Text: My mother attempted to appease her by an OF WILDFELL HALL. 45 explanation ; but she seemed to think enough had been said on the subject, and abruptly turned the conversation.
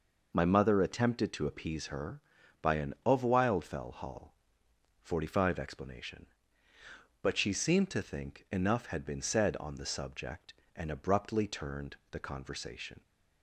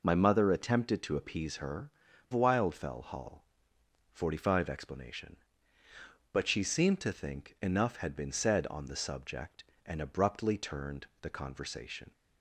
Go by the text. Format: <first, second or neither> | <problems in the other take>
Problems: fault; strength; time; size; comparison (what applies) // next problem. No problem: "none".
first | skips "by an OF"; at 2.1 s